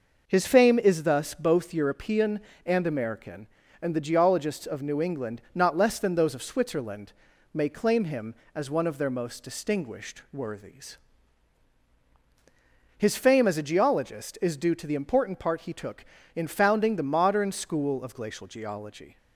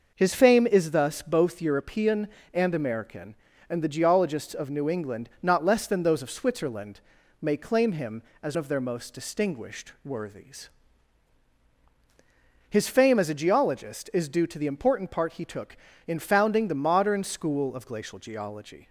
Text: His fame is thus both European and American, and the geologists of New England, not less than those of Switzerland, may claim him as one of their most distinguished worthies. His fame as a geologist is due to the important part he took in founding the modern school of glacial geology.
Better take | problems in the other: first | skips "one"; at 8.5 s

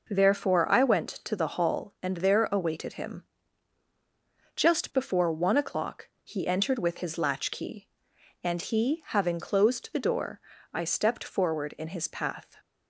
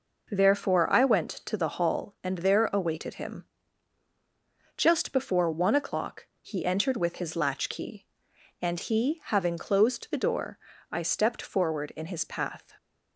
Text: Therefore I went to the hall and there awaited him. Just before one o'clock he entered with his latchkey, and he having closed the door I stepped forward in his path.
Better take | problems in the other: neither | pauses between "o'clock" and "he"; slight; the same in both // pauses between "door" and "I"; slight; the same in both

